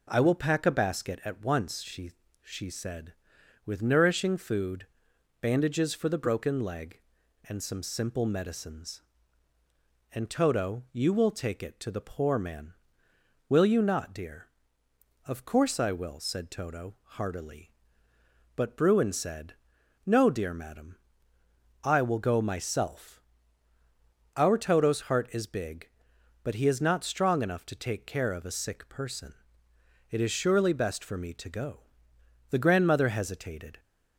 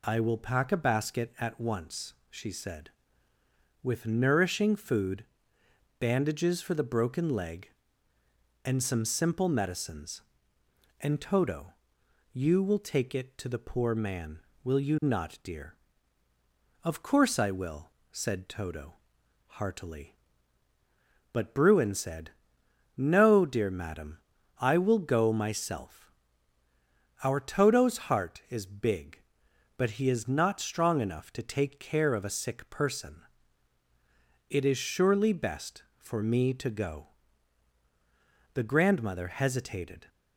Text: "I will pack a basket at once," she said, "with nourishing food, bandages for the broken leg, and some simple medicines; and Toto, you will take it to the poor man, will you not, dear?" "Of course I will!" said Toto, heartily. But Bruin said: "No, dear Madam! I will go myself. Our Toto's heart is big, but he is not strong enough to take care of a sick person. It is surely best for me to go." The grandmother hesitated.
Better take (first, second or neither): second